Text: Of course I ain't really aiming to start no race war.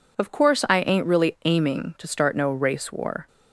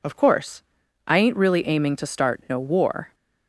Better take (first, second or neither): first